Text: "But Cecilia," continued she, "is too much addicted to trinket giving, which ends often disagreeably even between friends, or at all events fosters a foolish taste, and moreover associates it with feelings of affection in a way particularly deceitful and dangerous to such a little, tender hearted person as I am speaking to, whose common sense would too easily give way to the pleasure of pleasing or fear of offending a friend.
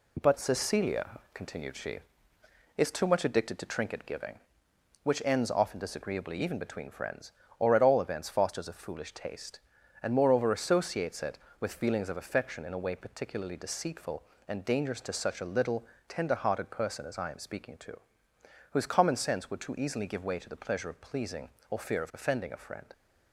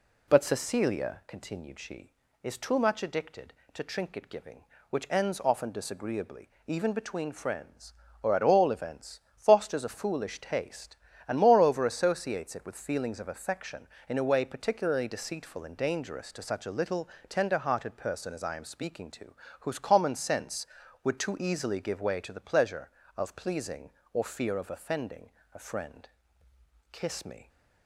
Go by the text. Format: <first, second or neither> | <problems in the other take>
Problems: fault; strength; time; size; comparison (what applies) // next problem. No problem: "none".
first | pauses between "disagreeably" and "even"; slight; at 6.5 s; 0.16 s long // pauses between "events" and "fosters"; slight; at 9.2 s; 0.18 s long // pauses between "offending" and "a"; slight; at 25.3 s; 0.24 s long // goes on to say "Kiss me"; from 26.9 s on; 0.56 s long